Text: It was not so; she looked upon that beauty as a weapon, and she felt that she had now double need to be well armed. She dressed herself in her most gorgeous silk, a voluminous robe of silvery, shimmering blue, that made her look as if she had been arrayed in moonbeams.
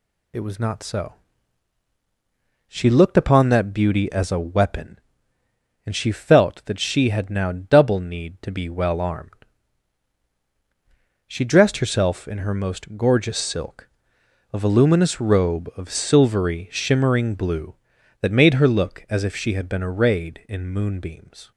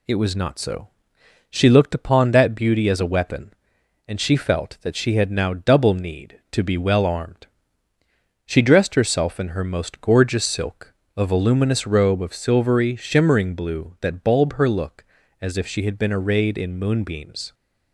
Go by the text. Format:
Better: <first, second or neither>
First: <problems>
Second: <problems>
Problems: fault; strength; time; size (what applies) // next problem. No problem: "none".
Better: first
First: none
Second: says "bulb" for "made"; at 14.2 s